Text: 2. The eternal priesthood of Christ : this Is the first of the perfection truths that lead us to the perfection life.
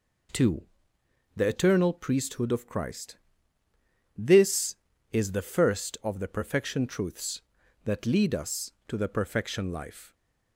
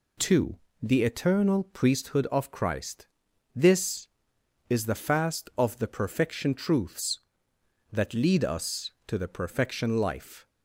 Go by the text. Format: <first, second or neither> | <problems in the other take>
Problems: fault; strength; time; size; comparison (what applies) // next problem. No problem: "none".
first | says "fast" for "first"; at 4.9 s